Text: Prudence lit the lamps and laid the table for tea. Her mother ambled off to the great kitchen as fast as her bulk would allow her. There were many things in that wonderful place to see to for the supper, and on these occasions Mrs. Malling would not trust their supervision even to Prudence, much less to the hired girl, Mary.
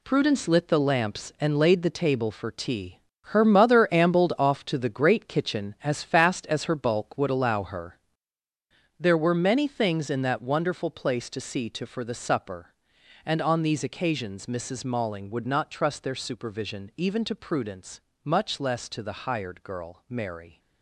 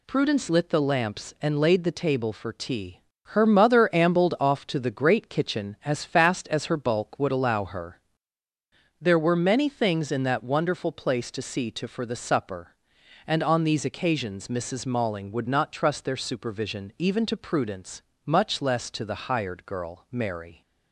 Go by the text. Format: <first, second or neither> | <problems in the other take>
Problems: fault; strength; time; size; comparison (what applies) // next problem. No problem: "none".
second | gets quieter; strong; throughout; 9 dB